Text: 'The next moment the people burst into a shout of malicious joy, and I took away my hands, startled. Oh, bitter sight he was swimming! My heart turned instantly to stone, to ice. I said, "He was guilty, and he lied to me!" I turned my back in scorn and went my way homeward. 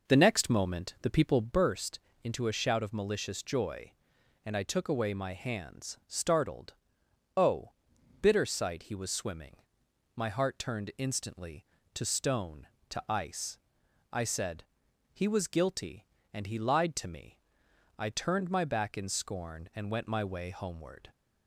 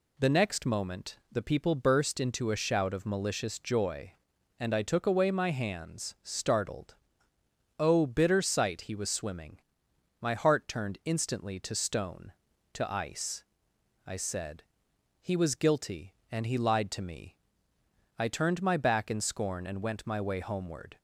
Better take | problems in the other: second | starts louder than the rest; noticeable; until 1.6 s; 5 dB // pauses between "burst" and "into"; slight; at 1.9 s; 0.24 s long

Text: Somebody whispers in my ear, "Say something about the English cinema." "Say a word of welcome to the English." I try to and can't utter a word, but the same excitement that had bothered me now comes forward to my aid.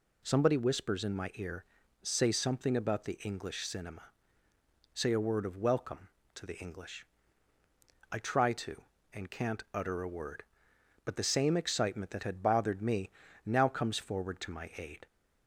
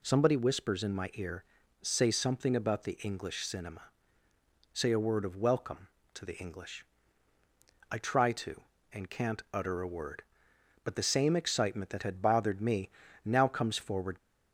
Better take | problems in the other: first | pauses between "me" and "now"; slight; at 12.8 s; 0.34 s long; slight in the first // stops before "to my aid"; at 14.1 s

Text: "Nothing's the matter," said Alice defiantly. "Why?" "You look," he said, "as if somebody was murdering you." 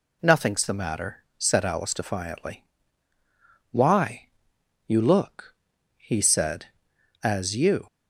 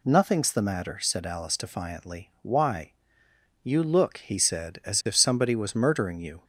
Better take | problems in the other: second | skips "if somebody was murdering"; at 7.5 s

